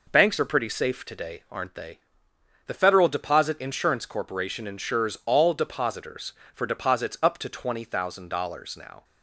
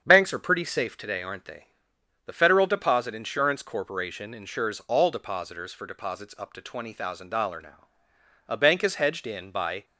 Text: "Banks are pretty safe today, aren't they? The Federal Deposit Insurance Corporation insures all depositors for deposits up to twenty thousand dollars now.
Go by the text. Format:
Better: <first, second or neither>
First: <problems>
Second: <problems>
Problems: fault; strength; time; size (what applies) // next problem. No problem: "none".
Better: first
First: none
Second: starts louder than the rest; strong; until 1.0 s; 7.5 dB // goes on to say "A bank is hedged in by"; from 8.4 s on; 1.3 s long